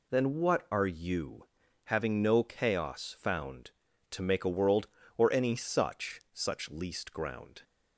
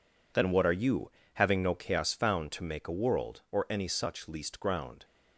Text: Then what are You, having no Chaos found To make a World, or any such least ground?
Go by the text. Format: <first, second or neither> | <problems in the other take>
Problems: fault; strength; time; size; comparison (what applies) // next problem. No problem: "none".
second | says "such" twice; at 6.3 s